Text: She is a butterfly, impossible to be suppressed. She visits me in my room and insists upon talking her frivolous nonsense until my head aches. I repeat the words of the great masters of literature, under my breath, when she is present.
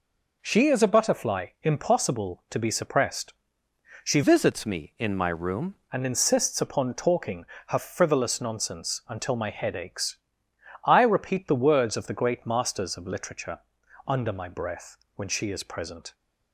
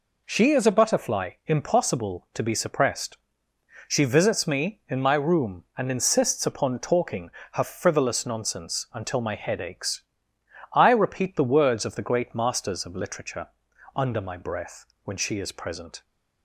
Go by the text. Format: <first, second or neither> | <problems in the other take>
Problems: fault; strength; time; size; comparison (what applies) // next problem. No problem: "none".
second | changes voice from "visits" to "room"; from 4.2 to 5.7 s; 1.5 s long // pauses between "talking" and "her"; slight; at 7.4 s; 0.24 s long; slight in the second